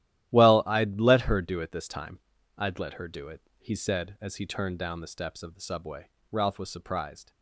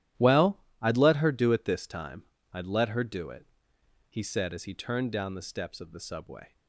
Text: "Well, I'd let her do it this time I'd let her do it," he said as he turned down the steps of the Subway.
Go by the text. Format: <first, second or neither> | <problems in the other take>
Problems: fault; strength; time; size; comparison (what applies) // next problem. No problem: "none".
second | starts louder than the rest; strong; until 1.3 s; 13 dB; strong in the second // pauses between "time" and "I'd"; at 2.1 s; 0.40 s long; slight in the second // goes on to say "Ralph was surprised"; noticeable; from 6.3 s on; 0.98 s long